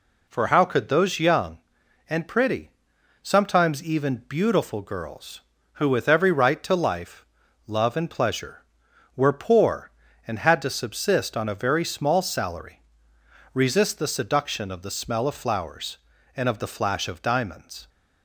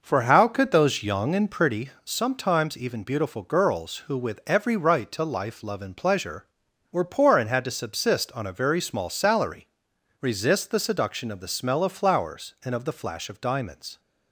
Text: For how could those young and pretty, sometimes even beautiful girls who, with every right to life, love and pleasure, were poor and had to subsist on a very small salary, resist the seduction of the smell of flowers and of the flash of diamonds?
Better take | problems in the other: first | starts louder than the rest; noticeable; until 1.8 s; 5.5 dB

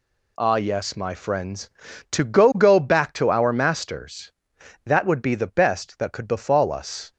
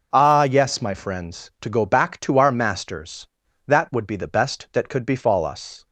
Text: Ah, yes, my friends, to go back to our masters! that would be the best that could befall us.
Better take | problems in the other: second | says "go" twice; at 2.5 s

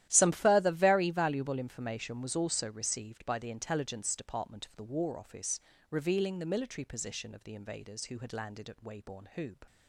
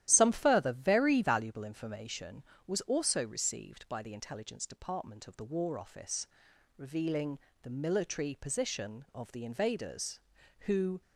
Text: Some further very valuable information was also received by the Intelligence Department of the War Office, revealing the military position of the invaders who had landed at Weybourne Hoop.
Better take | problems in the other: first | starts louder than the rest; strong; until 1.0 s; 12 dB; strong in the first // pauses between "revealing" and "the"; slight; at 7.3 s; 0.24 s long // stops before "had landed at Weybourne Hoop"; at 11.0 s

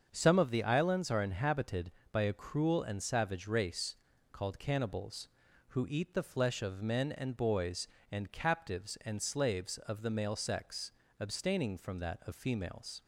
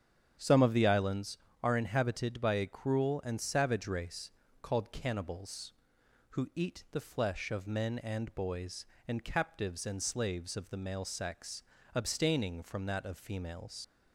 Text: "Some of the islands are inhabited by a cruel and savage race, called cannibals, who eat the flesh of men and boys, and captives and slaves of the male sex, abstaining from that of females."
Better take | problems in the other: first | starts louder than the rest; strong; until 1.6 s; 9 dB; also in the first // leaves "females" unfinished; at 13.8 s; 90 ms

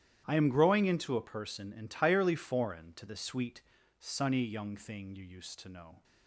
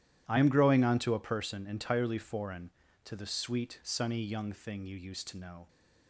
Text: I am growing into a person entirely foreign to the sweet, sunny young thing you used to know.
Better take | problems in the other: first | starts louder than the rest; strong; until 1.2 s; 12 dB; strong in the first // says "onto" for "into"; at 0.8 s

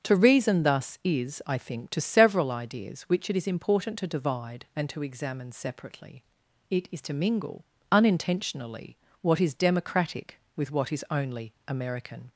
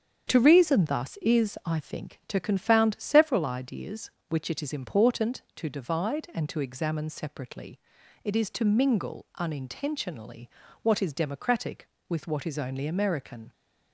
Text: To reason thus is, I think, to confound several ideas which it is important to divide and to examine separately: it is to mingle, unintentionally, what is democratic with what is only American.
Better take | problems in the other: second | starts louder than the rest; strong; until 1.1 s; 7.5 dB; strong in the second // skips "confound"; at 1.9 s // pauses between "only" and "American"; slight; at 11.5 s; 0.16 s long

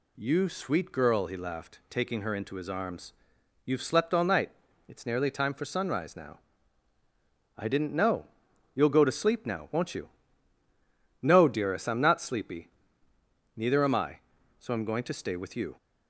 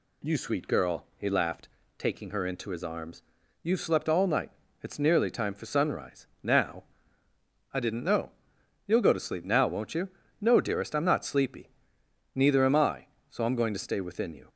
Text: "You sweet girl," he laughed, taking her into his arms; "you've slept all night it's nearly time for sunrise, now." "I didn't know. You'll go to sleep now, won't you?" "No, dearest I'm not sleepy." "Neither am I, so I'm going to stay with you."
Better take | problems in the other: first | pauses between "night" and "it's"; slight; at 4.5 s; 0.30 s long; slight in the first // says "within" for "with"; at 13.9 s

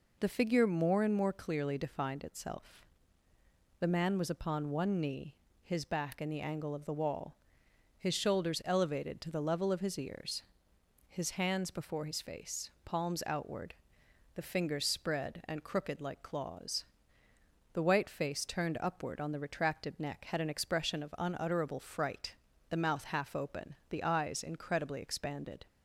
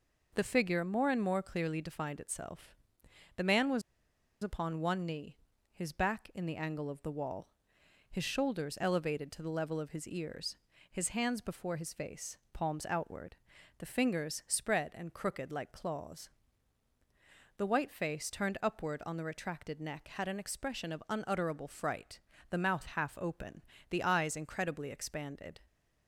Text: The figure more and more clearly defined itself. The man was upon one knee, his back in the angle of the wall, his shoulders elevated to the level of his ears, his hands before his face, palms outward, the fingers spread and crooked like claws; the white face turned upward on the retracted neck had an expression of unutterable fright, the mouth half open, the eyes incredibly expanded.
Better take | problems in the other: first | pauses between "was" and "upon"; noticeable; at 3.8 s; 0.61 s long

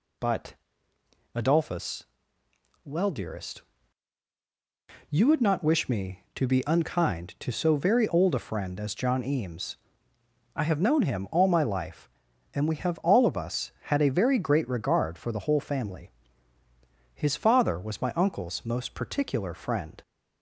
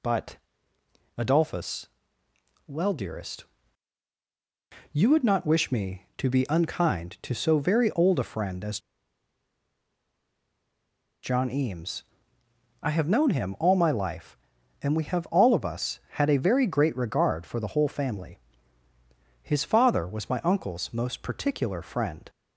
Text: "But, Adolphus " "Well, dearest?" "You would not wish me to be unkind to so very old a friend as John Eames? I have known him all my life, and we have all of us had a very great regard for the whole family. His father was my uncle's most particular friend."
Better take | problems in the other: first | pauses between "as" and "John"; strong; at 8.7 s; 2.4 s long

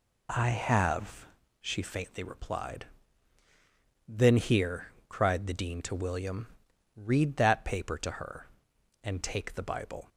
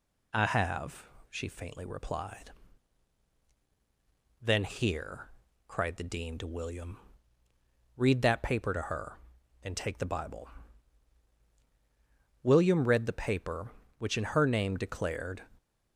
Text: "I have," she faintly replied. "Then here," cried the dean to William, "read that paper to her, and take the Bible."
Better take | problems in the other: first | goes on to say "William read the paper which in her name declared"; strong; from 12.4 s on; 3.0 s long

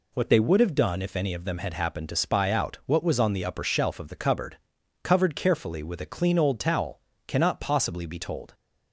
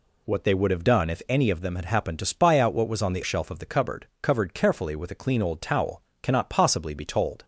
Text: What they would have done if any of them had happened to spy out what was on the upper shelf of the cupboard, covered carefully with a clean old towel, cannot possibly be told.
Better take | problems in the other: first | skips "upper"; at 3.2 s

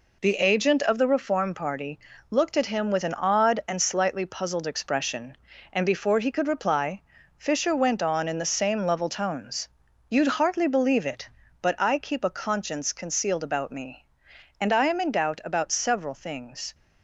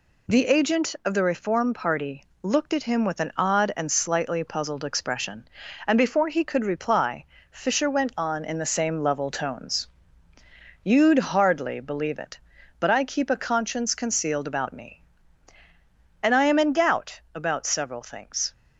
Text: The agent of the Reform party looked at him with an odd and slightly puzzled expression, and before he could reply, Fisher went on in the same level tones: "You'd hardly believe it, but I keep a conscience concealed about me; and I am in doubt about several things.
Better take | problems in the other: neither | pauses between "party" and "looked"; slight; the same in both

